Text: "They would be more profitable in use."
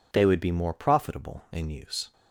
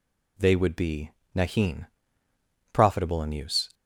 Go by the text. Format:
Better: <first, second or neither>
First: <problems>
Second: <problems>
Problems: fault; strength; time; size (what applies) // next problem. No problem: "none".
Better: first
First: none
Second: says "nahin" for "more"; at 1.3 s